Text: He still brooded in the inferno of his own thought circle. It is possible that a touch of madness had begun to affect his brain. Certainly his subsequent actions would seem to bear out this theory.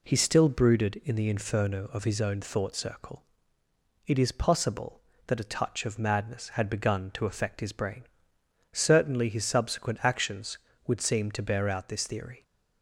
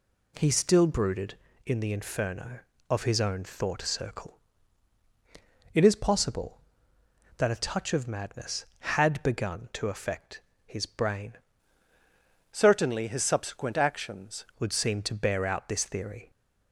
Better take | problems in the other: first | pauses between "affect" and "his"; slight; at 10.4 s; 0.26 s long // changes voice from "Certainly" to "actions"; from 12.5 to 14.4 s; 1.9 s long

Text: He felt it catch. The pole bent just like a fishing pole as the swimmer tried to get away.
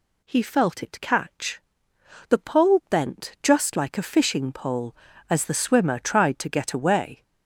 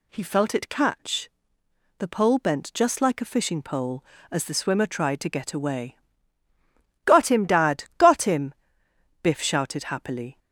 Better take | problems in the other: first | goes on to say "Got him Dad Got him Biff shouted happily"; strong; from 7.0 s on; 3.3 s long

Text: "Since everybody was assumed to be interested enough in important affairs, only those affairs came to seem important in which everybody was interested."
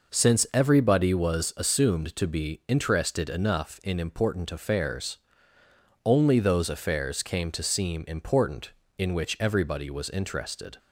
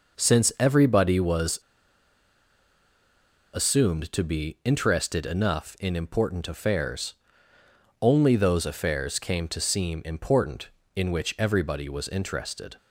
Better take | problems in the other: first | pauses between "was" and "assumed"; strong; at 1.5 s; 1.9 s long

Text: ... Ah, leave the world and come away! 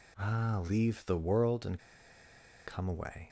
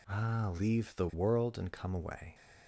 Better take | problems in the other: second | pauses between "and" and "come"; noticeable; at 1.7 s; 0.86 s long

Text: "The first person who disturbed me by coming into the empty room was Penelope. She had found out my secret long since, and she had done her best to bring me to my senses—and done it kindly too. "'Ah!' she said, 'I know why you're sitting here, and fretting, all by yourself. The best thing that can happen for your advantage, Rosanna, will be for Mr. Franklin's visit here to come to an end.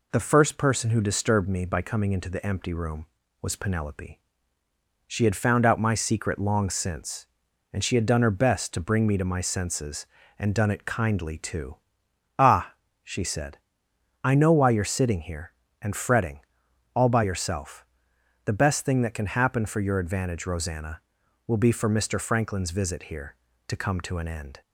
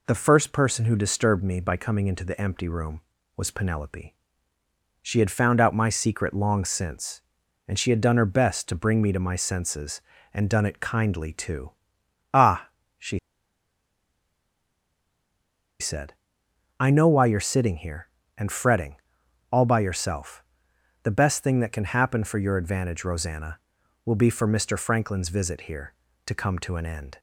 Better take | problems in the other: first | pauses between "she" and "said"; strong; at 13.1 s; 2.6 s long

